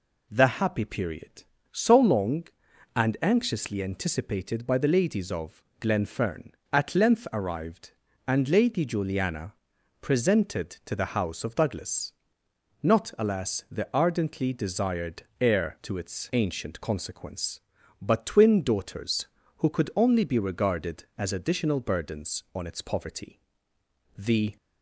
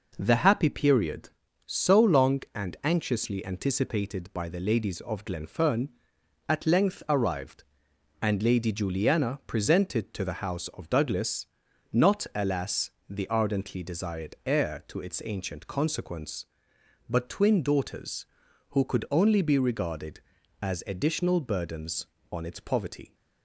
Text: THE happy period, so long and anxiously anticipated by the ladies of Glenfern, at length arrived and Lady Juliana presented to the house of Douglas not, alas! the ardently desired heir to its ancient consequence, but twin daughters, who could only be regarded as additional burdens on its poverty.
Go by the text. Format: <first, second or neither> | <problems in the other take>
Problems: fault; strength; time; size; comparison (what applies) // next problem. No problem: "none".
second | pauses between "of" and "Glenfern"; slight; at 5.6 s; 0.18 s long // pauses between "Juliana" and "presented"; noticeable; at 9.5 s; 0.48 s long // pauses between "Douglas" and "not"; noticeable; at 12.1 s; 0.74 s long; noticeable in the second // pauses between "desired" and "heir"; slight; at 15.2 s; 0.18 s long // goes on to say "The"; slight; from 24.1 s on; 0.38 s long